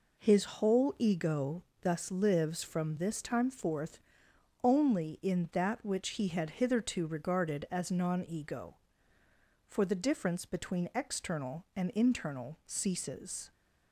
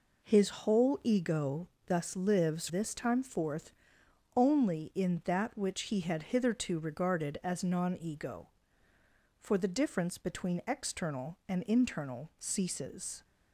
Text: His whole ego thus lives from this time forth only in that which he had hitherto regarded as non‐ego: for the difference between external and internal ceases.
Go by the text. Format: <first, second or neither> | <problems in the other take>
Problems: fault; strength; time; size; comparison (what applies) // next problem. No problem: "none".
first | pauses between "ego" and "thus"; slight; at 1.6 s; 0.20 s long; slight in the first // skips "from"; at 2.6 s // pauses between "forth" and "only"; noticeable; at 3.7 s; 0.64 s long; noticeable in the first